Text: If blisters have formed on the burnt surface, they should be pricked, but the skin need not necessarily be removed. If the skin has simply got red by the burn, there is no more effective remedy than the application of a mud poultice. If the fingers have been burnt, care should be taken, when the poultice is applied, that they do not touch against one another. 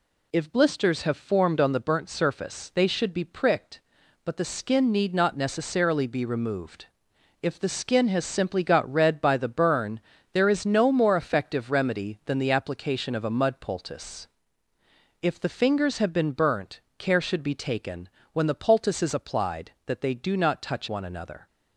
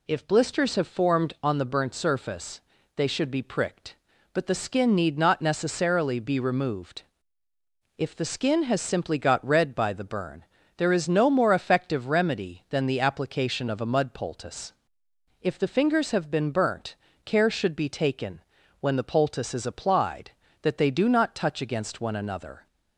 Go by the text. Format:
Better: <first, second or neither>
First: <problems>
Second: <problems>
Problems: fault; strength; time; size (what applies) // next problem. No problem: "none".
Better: second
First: skips "against"; at 20.8 s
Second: none